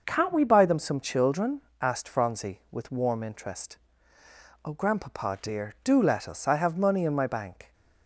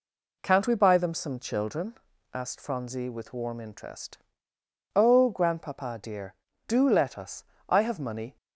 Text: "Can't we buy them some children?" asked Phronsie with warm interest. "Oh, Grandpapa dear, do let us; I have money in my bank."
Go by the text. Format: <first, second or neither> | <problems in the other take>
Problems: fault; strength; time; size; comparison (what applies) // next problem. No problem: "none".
first | stops before "in my bank"; at 8.3 s